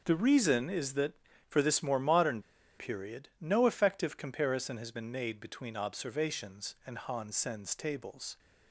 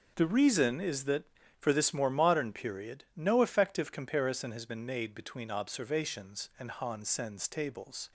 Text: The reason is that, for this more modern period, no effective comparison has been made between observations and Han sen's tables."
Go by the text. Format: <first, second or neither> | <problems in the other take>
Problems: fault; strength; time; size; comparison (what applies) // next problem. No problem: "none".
second | starts louder than the rest; until 1.0 s; 6.5 dB; also in the second // pauses between "modern" and "period"; at 2.4 s; 0.37 s long